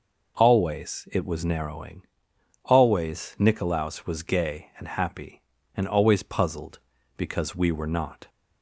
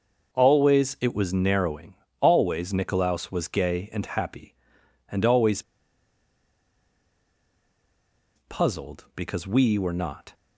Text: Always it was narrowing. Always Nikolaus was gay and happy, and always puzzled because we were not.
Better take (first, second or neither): first